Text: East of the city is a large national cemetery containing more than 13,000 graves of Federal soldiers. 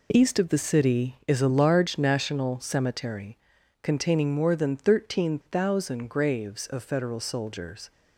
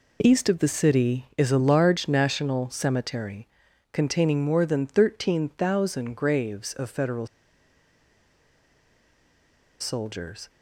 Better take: first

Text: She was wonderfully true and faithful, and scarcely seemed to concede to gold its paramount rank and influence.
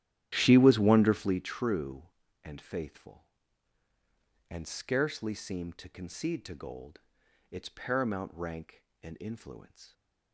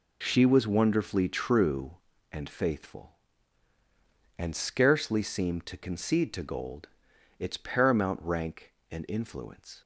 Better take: second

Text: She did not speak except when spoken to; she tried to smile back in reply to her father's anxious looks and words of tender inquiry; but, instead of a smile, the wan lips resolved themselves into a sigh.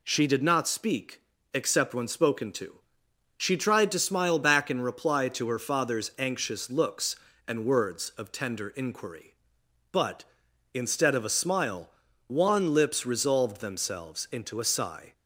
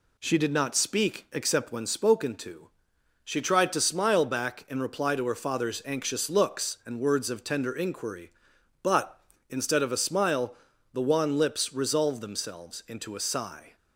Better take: second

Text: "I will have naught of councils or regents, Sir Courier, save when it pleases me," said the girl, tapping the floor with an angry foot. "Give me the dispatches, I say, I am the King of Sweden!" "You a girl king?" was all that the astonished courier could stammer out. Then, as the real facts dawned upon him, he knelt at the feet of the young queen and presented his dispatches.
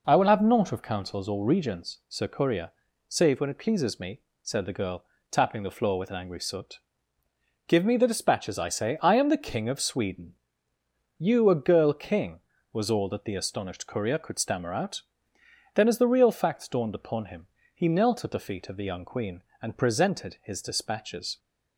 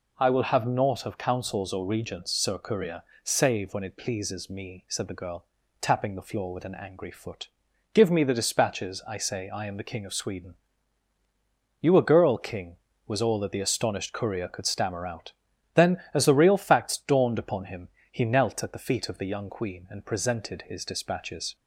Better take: second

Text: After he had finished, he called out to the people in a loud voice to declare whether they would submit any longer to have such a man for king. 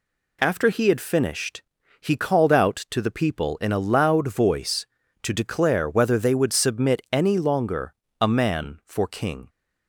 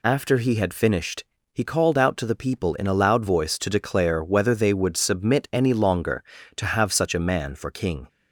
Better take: second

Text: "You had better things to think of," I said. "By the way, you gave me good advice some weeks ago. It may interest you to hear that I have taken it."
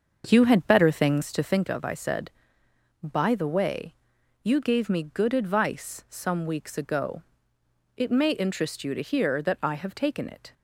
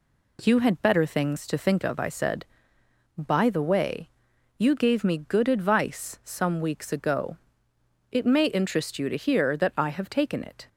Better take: second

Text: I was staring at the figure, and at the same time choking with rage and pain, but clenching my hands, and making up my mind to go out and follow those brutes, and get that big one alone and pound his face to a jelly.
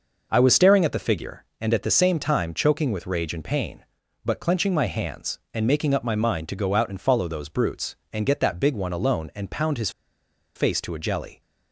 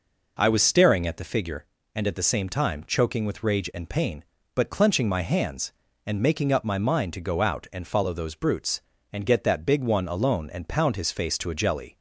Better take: second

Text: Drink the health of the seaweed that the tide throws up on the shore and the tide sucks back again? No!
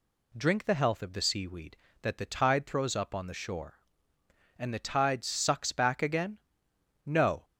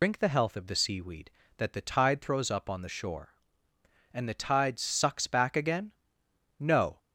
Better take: first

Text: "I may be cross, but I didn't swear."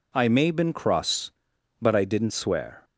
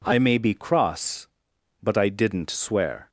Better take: second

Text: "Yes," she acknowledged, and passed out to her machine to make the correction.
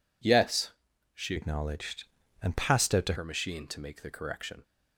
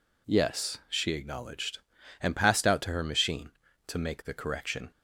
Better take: second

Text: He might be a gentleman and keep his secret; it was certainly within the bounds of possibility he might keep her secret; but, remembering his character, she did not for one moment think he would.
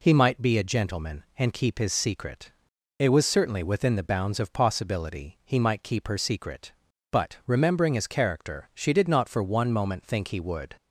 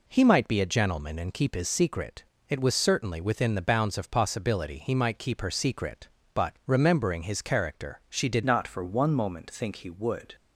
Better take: first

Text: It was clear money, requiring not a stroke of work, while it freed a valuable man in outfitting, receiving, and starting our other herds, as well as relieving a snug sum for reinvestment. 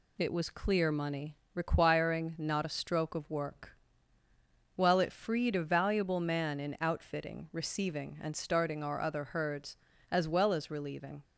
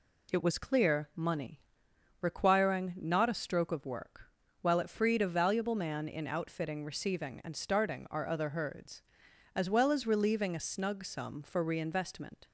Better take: second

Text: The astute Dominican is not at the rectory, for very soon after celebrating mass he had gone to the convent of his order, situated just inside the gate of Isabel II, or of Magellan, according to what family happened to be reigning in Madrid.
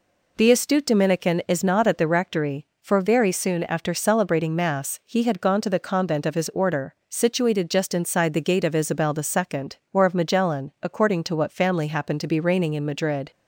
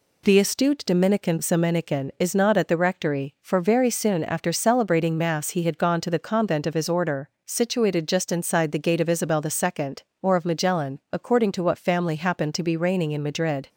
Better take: first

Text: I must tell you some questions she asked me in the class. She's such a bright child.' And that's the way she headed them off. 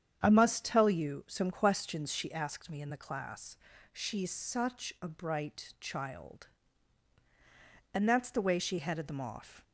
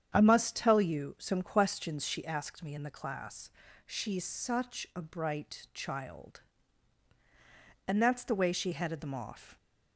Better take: neither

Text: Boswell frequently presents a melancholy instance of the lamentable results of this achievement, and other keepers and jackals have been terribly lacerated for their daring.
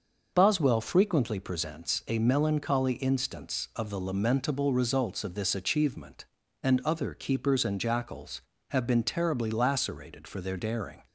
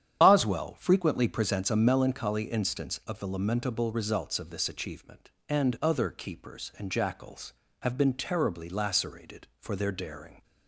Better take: first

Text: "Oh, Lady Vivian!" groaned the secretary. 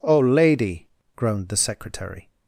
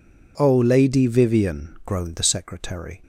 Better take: second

